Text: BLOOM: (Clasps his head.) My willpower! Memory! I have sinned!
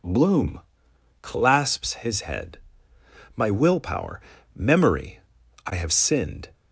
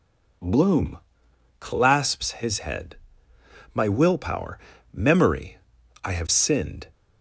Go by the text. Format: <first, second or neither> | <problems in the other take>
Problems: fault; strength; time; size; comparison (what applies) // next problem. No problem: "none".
neither | none